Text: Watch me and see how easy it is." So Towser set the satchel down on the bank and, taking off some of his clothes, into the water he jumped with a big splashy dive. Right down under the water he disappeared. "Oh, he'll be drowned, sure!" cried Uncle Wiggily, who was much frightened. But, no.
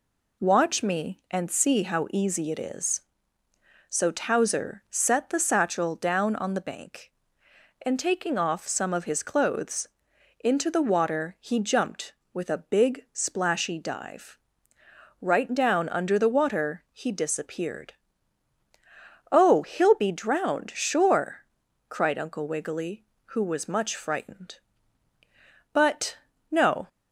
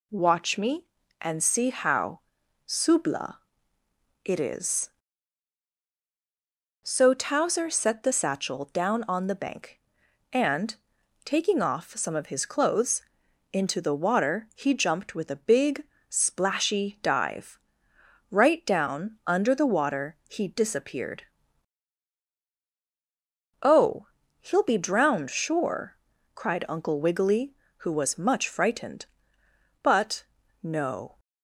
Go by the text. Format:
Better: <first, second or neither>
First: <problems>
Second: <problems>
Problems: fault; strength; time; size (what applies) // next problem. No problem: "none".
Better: first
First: none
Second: says "subla" for "easy"; at 2.6 s // pauses between "big" and "splashy"; slight; at 15.8 s; 0.26 s long